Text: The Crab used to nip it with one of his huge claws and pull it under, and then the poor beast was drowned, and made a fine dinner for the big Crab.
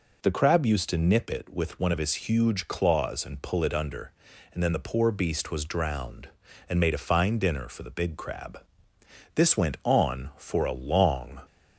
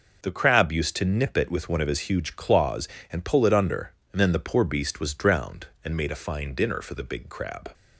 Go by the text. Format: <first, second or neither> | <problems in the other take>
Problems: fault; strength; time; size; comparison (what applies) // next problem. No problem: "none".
second | goes on to say "This went on for a long"; strong; from 9.3 s on; 2.0 s long